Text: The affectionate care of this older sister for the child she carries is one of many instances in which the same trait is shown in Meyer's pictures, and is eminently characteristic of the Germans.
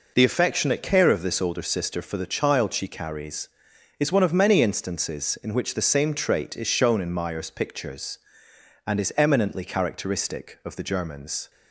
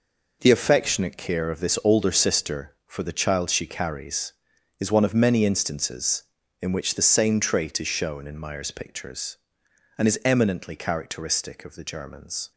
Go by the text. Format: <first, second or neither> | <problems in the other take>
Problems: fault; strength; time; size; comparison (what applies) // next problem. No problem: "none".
neither | none